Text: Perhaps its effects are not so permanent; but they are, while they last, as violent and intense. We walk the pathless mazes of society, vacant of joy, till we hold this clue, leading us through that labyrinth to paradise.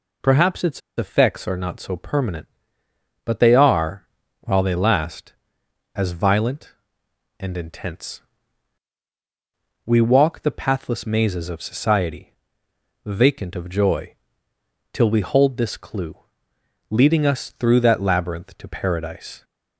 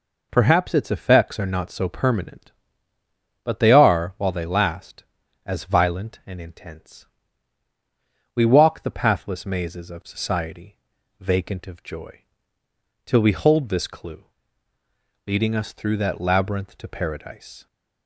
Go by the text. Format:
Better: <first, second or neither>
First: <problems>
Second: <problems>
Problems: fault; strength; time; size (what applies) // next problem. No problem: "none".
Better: second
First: pauses between "its" and "effects"; slight; at 0.8 s; 0.17 s long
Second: none